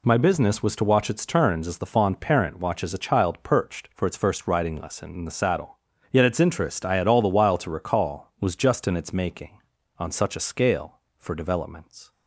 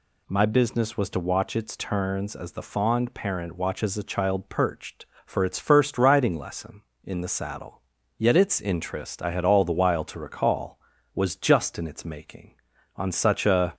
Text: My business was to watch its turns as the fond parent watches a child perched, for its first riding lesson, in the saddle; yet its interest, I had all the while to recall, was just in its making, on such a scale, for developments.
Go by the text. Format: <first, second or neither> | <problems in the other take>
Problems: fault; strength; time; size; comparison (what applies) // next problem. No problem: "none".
first | stops before "scale for developments"; at 13.7 s